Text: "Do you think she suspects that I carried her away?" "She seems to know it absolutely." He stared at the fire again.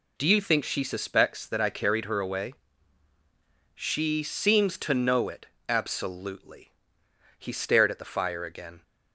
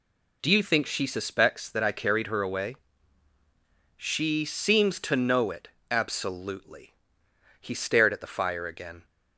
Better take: neither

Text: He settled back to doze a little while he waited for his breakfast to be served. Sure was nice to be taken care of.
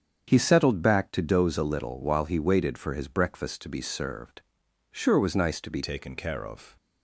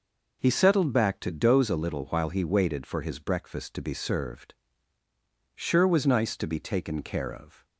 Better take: second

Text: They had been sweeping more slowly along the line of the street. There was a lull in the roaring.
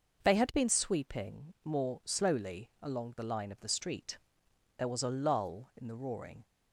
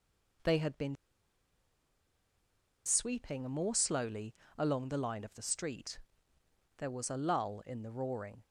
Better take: first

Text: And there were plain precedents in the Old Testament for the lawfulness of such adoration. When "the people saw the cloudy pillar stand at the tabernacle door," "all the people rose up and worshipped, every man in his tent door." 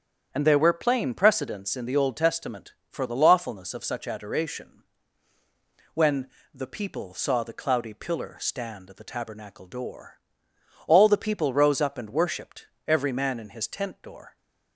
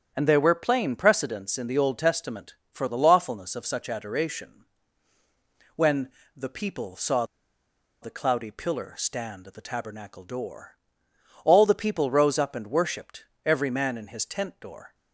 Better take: first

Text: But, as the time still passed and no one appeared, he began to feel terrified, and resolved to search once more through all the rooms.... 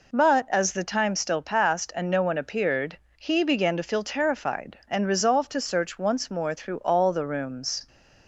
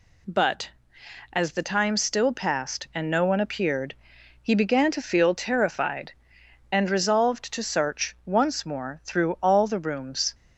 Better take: neither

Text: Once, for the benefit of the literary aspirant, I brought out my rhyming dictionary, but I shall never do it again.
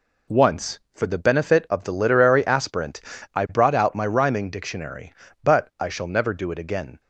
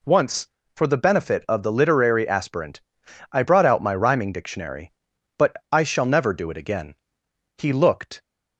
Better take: first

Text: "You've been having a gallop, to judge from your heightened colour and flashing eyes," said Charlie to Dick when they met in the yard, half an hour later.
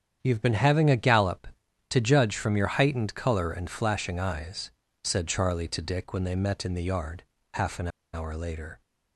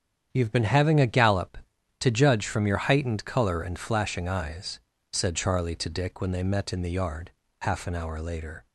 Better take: second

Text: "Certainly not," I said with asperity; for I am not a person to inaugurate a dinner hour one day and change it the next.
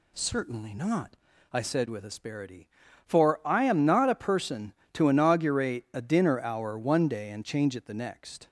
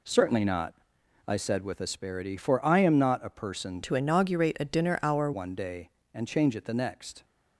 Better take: first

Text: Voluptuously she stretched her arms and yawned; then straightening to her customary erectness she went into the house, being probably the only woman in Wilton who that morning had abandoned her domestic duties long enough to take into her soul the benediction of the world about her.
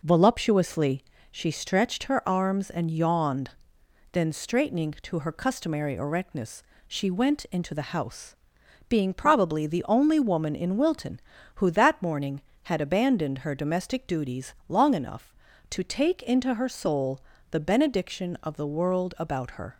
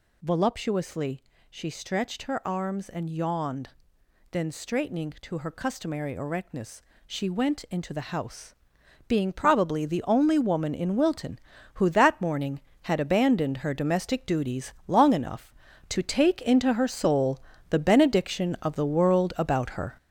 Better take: first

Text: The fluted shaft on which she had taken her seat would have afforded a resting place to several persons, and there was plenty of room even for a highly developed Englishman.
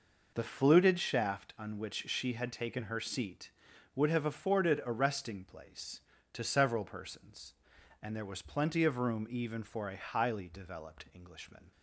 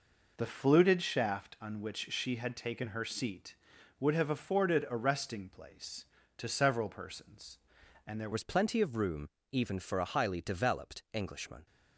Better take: first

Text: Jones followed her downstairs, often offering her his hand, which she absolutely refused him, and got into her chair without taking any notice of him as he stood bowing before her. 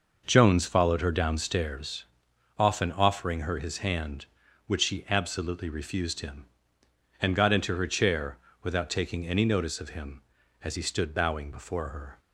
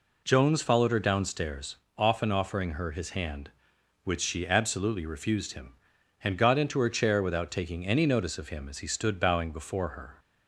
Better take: second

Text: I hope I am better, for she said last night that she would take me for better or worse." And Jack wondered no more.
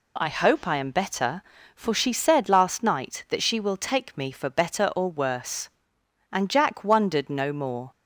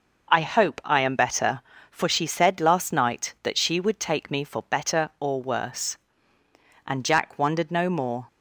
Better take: second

